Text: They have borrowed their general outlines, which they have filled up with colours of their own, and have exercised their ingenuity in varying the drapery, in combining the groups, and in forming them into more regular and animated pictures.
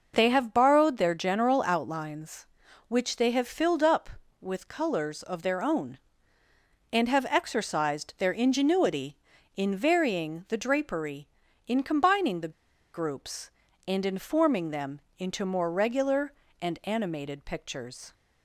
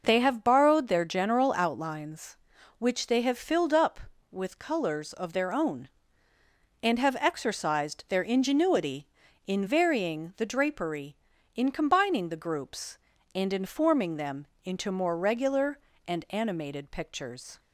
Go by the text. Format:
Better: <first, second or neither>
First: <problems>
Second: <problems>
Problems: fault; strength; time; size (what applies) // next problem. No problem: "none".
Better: second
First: pauses between "the" and "groups"; at 12.5 s; 0.42 s long // pauses between "them" and "into"; slight; at 15.0 s; 0.16 s long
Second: pauses between "them" and "into"; slight; at 14.4 s; 0.16 s long